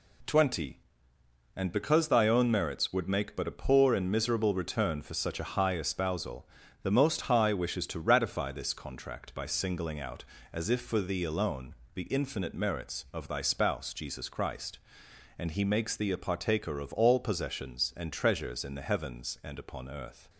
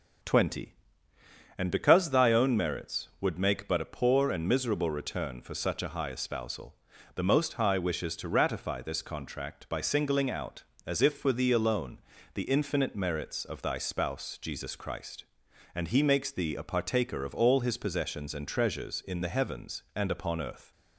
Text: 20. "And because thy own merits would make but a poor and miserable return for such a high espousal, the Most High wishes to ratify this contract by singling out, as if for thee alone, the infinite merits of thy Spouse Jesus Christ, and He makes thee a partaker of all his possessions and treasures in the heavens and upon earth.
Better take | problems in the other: second | skips "his"; at 17.1 s

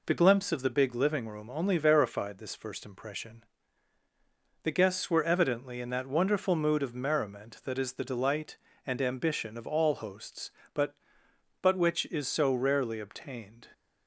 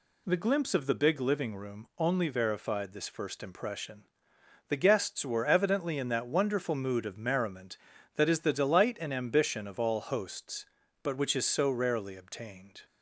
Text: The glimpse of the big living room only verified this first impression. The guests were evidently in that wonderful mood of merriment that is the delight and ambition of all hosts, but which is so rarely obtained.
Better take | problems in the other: second | says "but" twice; at 11.6 s

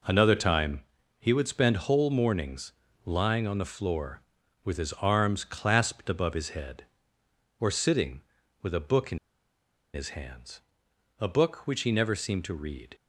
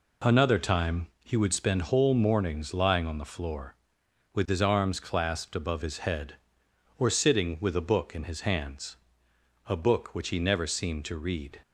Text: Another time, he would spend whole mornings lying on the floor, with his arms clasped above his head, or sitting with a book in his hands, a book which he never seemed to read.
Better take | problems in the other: second | pauses between "mornings" and "lying"; slight; at 2.7 s; 0.32 s long // pauses between "in" and "his"; noticeable; at 9.1 s; 0.76 s long

